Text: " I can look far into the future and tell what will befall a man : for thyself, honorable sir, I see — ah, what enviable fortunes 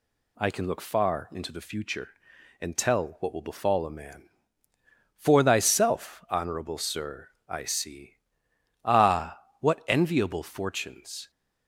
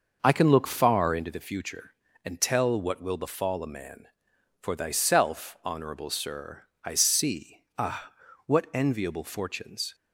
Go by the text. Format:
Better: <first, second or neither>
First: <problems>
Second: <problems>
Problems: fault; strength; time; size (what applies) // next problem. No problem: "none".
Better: first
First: none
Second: starts louder than the rest; noticeable; until 1.4 s; 6 dB